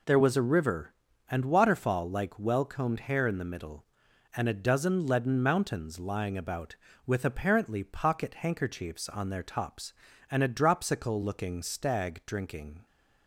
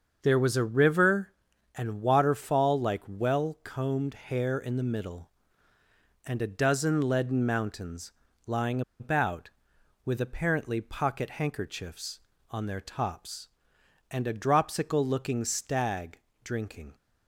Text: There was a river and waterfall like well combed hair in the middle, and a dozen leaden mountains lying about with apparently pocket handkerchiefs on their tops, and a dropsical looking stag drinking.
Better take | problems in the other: first | starts louder than the rest; until 1.2 s; 6.5 dB // pauses between "mountains" and "lying"; slight; at 8.1 s; 0.34 s long // pauses between "lying" and "about"; slight; at 8.8 s; 0.18 s long // pauses between "stag" and "drinking"; slight; at 16.1 s; 0.24 s long

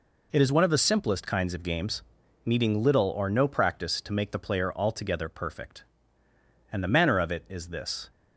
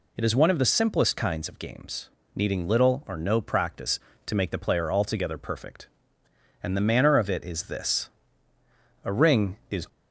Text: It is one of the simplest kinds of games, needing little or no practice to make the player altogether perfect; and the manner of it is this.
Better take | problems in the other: first | goes on to say "A ring is"; noticeable; from 9.0 s on; 0.84 s long

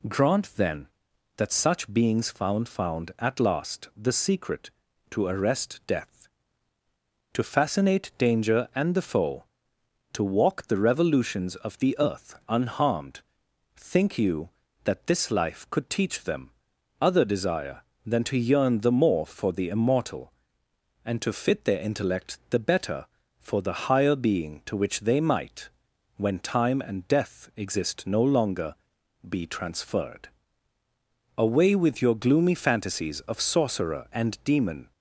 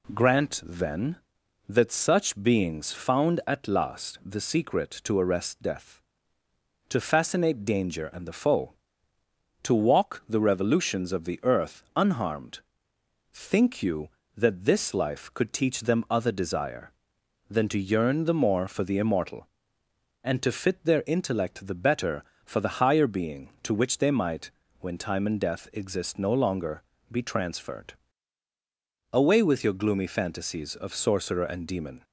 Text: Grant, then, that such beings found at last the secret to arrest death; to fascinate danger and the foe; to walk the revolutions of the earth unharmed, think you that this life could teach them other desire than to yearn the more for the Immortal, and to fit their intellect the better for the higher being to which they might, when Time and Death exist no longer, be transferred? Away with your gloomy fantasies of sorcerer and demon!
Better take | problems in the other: second | says "found" twice; at 2.6 s // pauses between "them" and "other"; noticeable; at 16.4 s; 0.50 s long

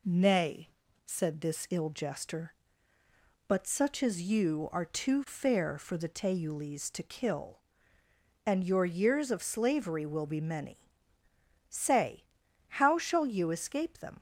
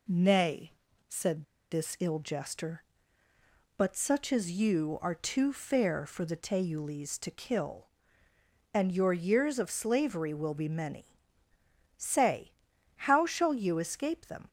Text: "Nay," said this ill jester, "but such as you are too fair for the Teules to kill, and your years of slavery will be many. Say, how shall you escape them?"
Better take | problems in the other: first | pauses between "said" and "this"; slight; at 1.4 s; 0.27 s long

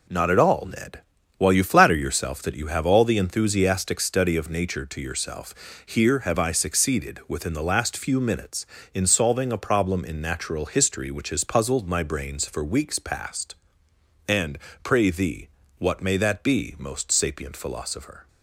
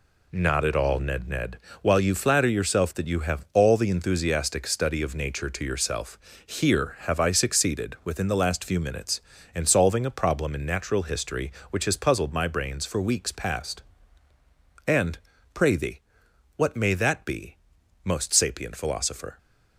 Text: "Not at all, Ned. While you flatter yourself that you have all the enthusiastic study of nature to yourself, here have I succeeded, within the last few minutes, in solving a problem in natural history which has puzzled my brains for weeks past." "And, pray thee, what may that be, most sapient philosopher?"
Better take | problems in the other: first | says "Ned" twice; at 1.2 s

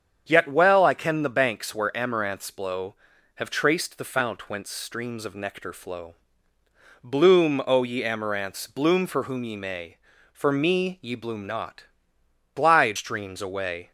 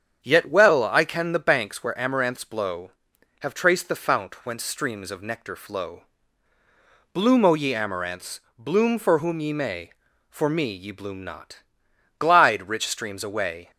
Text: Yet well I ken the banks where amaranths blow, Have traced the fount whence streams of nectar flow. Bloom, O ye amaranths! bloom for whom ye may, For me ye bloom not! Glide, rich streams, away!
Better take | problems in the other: second | starts louder than the rest; strong; until 1.2 s; 7.5 dB; strong in the second // skips "rich"; at 12.9 s

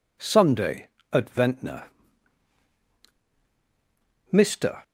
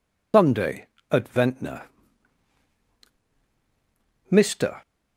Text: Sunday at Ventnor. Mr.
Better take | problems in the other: first | loses the start of "Sunday"; at 0.3 s; 155 ms

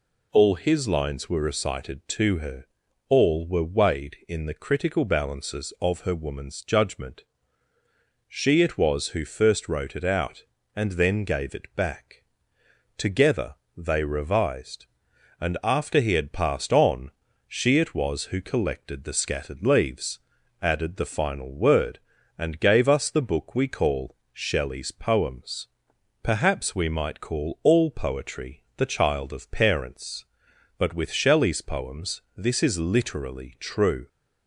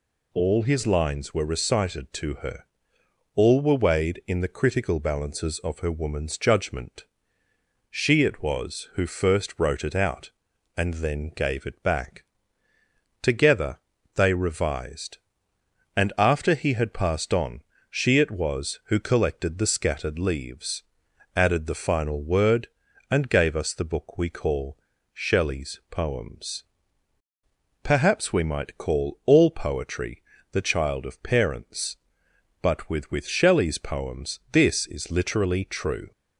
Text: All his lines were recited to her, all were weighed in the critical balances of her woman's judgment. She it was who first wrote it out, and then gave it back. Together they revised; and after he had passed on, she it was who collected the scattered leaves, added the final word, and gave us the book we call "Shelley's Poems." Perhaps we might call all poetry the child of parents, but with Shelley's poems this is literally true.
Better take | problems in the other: first | pauses between "Together" and "they"; slight; at 13.7 s; 0.36 s long; slight in the first // pauses between "call" and "Shelley's"; slight; at 24.7 s; 0.36 s long; slight in the first // pauses between "poetry" and "the"; slight; at 30.2 s; 0.30 s long // says "with" twice; at 33.0 s

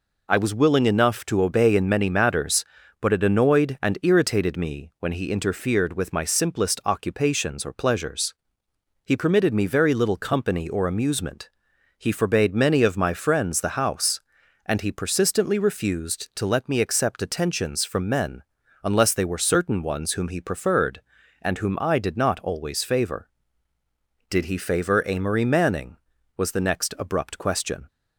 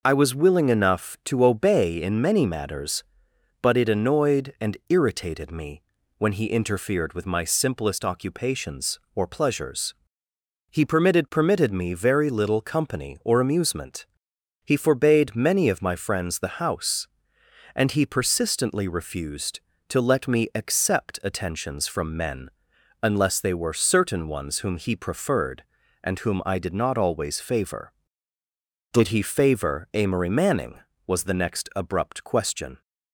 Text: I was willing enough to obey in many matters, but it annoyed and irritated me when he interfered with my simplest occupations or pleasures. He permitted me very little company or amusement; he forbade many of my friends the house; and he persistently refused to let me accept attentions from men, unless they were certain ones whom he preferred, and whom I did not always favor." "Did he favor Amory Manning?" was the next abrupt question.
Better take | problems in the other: first | pauses between "me" and "when"; at 5.8 s; 0.38 s long // says "permitted" twice; at 11.3 s

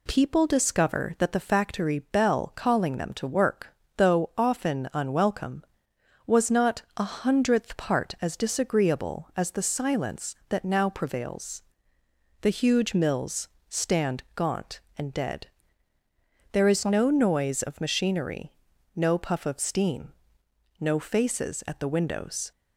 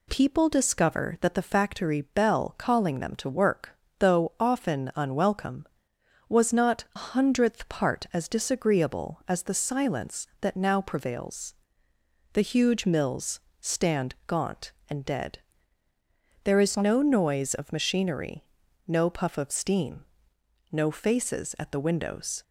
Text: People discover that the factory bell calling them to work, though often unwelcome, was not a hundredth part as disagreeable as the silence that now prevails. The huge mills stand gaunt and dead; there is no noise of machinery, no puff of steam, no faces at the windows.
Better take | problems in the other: first | skips "a"; at 6.9 s // pauses between "mills" and "stand"; slight; at 13.3 s; 0.22 s long; slight in the first

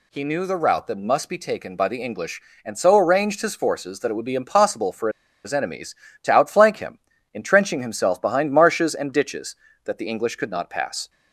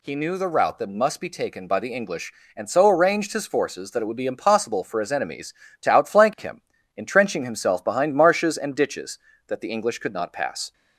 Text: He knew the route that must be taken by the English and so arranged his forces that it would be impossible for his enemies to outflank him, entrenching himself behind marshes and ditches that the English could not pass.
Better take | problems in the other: second | pauses between "for" and "his"; slight; at 5.0 s; 0.35 s long

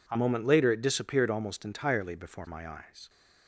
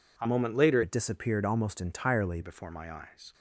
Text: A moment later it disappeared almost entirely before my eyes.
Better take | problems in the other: first | changes voice from "it" to "entirely"; from 0.8 to 2.3 s; 1.5 s long

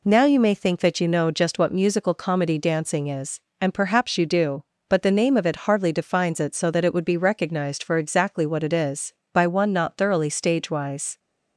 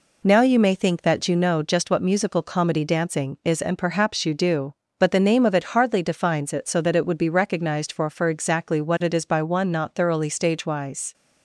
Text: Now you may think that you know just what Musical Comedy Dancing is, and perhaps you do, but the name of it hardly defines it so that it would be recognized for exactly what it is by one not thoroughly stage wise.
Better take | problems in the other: first | says "for" twice; at 8.0 s

